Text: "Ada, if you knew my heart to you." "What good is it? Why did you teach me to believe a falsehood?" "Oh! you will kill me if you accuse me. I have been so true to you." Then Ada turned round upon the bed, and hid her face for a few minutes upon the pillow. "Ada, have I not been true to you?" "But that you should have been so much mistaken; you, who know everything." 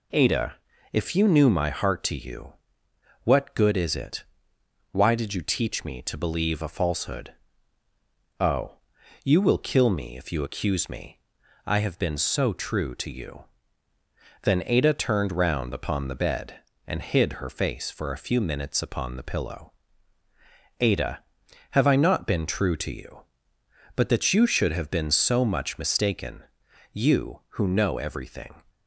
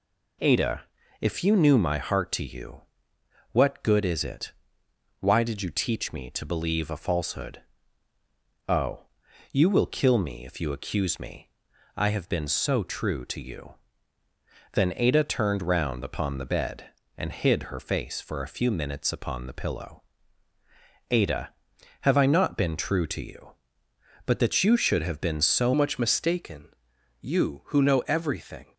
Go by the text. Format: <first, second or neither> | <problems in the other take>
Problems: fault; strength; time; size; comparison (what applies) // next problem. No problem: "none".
first | changes voice at "much"; from 25.7 s on; 3.0 s long